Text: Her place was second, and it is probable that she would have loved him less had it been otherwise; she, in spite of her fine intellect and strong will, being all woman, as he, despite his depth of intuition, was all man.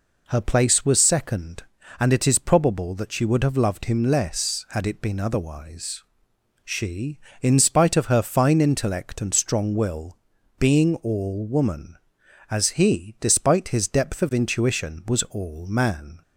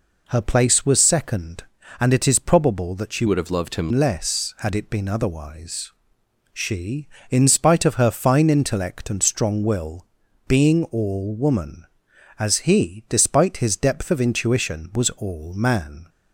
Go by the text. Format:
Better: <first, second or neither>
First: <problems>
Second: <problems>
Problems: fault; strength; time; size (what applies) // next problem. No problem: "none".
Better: first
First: none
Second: changes voice from "would" to "him"; from 3.2 to 3.9 s; 0.7 s long